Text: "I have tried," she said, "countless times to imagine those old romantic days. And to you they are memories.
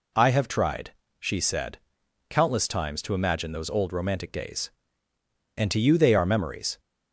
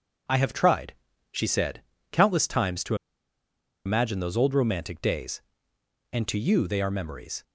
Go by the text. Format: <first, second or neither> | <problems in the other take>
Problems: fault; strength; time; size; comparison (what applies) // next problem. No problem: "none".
first | pauses between "to" and "imagine"; noticeable; at 2.9 s; 0.91 s long